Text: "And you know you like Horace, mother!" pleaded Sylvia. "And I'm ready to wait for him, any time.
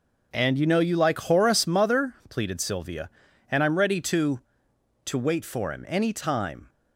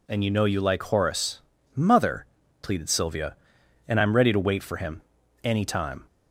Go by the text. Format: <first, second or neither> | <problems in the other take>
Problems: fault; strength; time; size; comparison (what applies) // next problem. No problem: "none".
second | says "to" twice; at 5.0 s